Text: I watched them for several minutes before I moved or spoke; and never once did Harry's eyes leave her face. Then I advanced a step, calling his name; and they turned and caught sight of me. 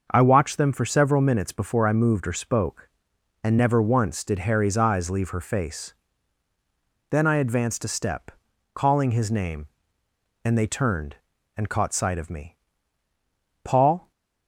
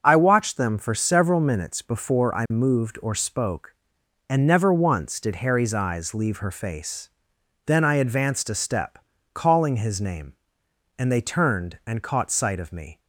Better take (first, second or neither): second